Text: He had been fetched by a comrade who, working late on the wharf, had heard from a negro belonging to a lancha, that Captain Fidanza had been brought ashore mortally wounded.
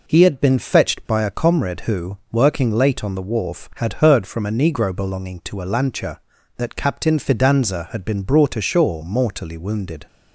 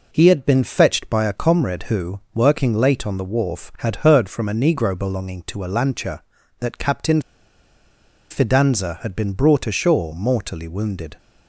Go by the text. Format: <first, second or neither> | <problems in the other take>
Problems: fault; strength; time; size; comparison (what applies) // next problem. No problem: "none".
first | pauses between "Captain" and "Fidanza"; at 7.2 s; 1.0 s long